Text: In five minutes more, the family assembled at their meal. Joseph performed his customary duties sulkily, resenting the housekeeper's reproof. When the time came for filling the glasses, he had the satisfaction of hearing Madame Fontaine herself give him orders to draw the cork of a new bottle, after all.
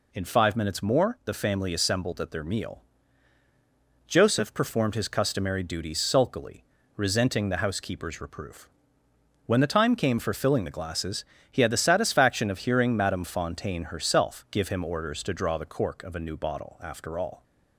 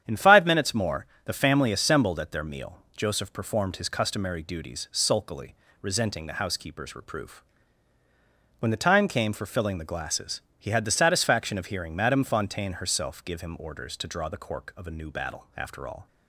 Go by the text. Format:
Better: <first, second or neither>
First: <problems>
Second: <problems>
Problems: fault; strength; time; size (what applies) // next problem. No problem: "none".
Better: first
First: none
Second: starts louder than the rest; strong; until 1.0 s; 9.5 dB // says "battle" for "bottle"; at 15.1 s